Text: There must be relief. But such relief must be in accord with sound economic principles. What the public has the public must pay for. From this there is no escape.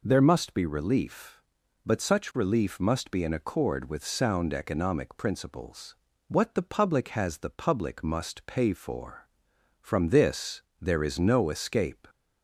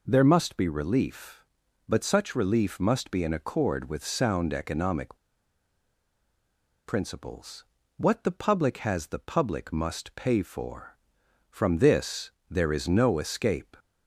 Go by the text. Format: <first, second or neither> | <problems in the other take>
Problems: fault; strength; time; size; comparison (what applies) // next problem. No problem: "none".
first | pauses between "economic" and "principles"; strong; at 5.1 s; 1.7 s long // pauses between "this" and "there"; slight; at 12.3 s; 0.18 s long; slight in the first